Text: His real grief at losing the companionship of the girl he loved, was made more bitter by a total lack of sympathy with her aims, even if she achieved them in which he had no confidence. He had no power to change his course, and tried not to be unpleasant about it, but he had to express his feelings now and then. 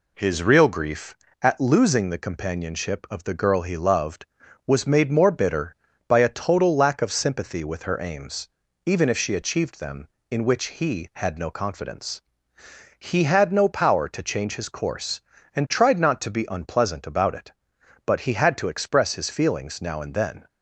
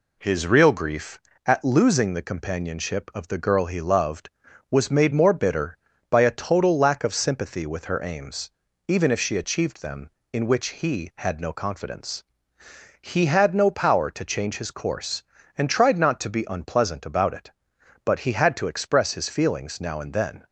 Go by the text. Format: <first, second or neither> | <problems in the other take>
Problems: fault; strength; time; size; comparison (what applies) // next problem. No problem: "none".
neither | none